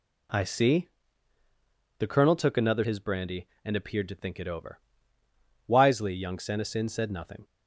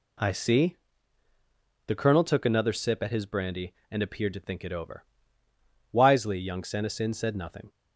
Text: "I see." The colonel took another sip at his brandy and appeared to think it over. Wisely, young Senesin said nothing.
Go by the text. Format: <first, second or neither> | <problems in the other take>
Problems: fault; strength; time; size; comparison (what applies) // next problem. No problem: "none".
second | skips "sip at"; at 2.8 s